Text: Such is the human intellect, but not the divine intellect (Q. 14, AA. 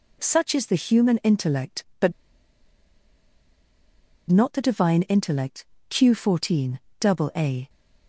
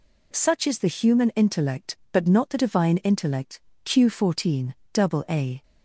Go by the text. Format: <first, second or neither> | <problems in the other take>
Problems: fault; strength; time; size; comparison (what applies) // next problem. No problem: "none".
second | pauses between "but" and "not"; strong; at 2.1 s; 2.1 s long